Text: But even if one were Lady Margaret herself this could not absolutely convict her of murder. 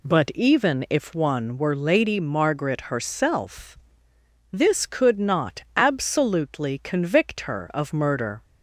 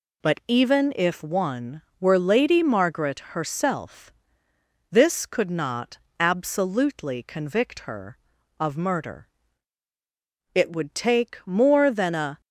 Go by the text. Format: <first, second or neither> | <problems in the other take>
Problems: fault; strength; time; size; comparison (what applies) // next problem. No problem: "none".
first | pauses between "herself" and "this"; noticeable; at 4.1 s; 0.80 s long; noticeable in the first // pauses between "not" and "absolutely"; slight; at 5.9 s; 0.20 s long // goes on to say "It would take more than a"; strong; from 10.5 s on; 1.8 s long